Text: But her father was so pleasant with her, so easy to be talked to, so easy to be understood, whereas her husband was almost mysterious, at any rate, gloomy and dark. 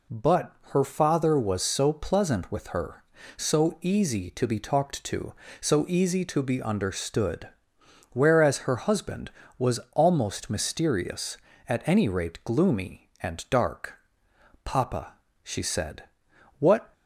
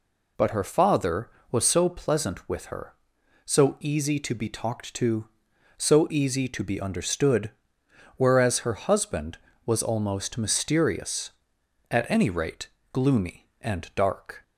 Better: second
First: pauses between "But" and "her"; slight; at 0.5 s; 0.20 s long // goes on to say "Papa she said what"; strong; from 14.6 s on; 2.2 s long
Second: none

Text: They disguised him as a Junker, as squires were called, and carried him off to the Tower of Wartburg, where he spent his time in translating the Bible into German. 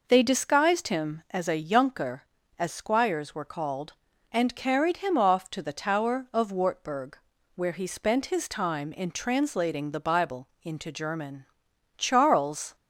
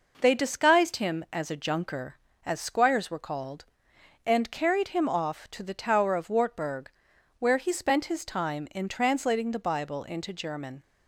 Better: second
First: pauses between "Bible" and "into"; slight; at 10.4 s; 0.16 s long // goes on to say "Charles"; noticeable; from 11.9 s on; 0.78 s long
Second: none

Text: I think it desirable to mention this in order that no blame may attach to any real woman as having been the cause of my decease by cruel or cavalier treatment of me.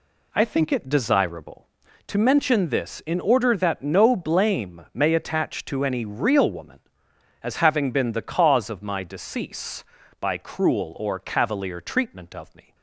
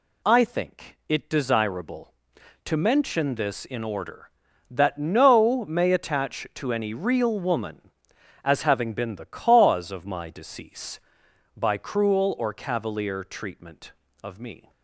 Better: first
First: none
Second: skips "blame"; at 5.6 s

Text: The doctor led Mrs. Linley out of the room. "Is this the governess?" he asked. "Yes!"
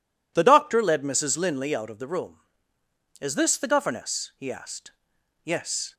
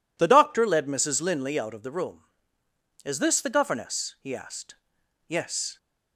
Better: neither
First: none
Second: none

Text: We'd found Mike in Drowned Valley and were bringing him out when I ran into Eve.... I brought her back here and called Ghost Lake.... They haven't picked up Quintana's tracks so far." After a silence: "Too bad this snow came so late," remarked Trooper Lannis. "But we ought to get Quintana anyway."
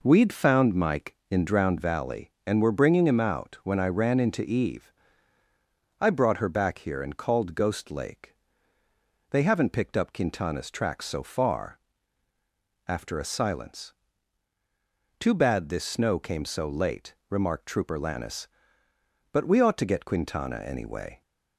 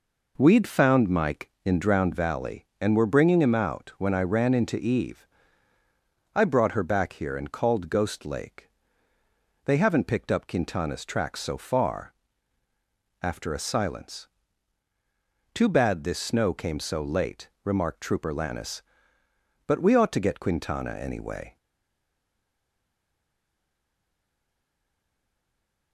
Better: first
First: none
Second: stays silent after the last word; strong; from 21.5 s on; 4.4 s long

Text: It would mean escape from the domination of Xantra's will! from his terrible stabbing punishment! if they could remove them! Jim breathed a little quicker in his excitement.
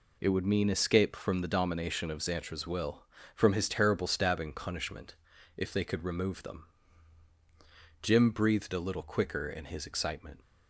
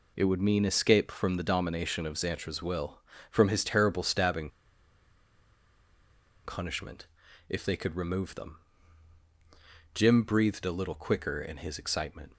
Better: first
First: none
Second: pauses between "stabbing" and "punishment"; strong; at 4.4 s; 1.9 s long

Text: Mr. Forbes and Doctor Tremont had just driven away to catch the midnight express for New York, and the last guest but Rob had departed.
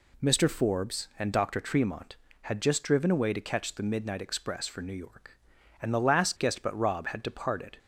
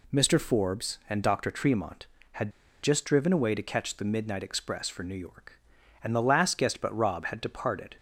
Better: first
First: none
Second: pauses between "had" and "just"; slight; at 2.5 s; 0.31 s long

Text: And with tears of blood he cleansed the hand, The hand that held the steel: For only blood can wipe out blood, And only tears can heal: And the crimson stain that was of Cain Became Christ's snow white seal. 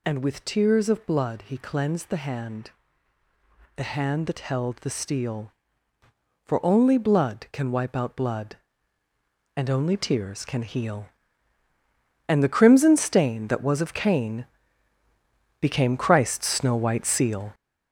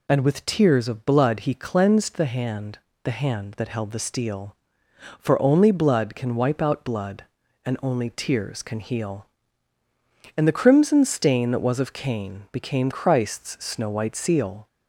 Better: second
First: gets louder; throughout; 7 dB // pauses between "Cain" and "Became"; at 14.4 s; 1.1 s long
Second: none

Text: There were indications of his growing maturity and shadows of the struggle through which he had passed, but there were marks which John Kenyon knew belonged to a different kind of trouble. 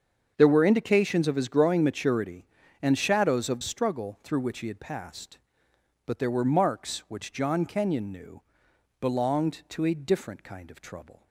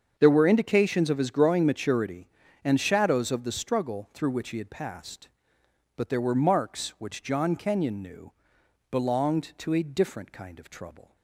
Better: second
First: starts louder than the rest; until 1.3 s; 7 dB // skips "the"; at 3.6 s // pauses between "knew" and "belonged"; noticeable; at 8.4 s; 0.60 s long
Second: starts louder than the rest; until 1.1 s; 7 dB // pauses between "knew" and "belonged"; noticeable; at 8.3 s; 0.60 s long

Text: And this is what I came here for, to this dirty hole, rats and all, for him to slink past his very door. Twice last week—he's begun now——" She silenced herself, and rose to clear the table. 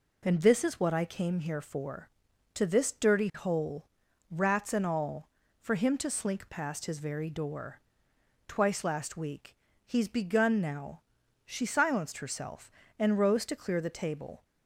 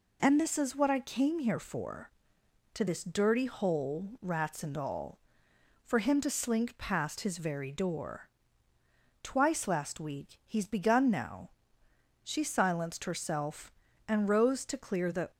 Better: first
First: none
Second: stops before "table"; at 15.3 s

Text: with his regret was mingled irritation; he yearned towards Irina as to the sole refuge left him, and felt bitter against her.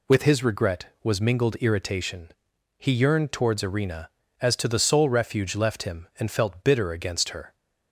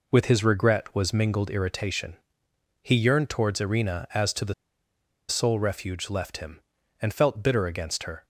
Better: first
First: none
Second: pauses between "the" and "sole"; noticeable; at 4.5 s; 0.75 s long

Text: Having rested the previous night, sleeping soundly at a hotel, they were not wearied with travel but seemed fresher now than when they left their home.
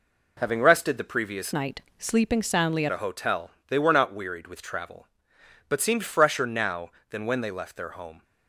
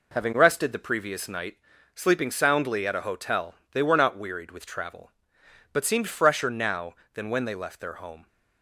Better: second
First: changes voice from "night" to "at"; from 1.5 to 2.8 s; 1.3 s long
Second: none

